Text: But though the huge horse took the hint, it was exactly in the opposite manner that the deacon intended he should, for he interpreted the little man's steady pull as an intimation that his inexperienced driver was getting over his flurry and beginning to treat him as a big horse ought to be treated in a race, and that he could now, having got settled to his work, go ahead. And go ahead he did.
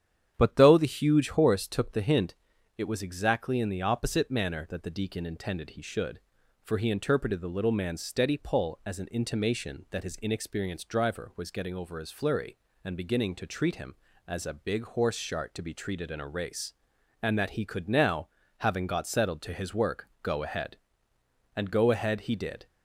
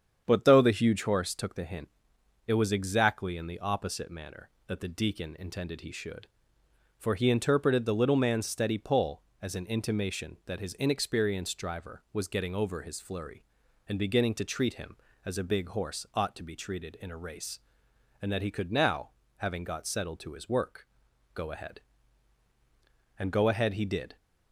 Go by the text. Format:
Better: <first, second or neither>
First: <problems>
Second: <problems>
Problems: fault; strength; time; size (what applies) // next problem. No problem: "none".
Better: second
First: starts louder than the rest; strong; until 1.3 s; 9 dB // says "shart" for "ought"; at 15.1 s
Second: starts louder than the rest; strong; until 1.2 s; 8 dB